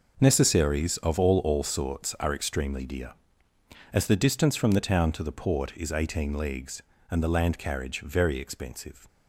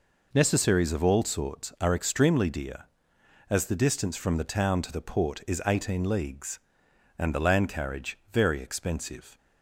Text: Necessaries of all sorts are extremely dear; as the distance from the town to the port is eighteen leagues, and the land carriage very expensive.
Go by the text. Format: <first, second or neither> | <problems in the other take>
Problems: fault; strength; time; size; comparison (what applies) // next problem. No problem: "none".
second | says "all" twice; at 1.4 s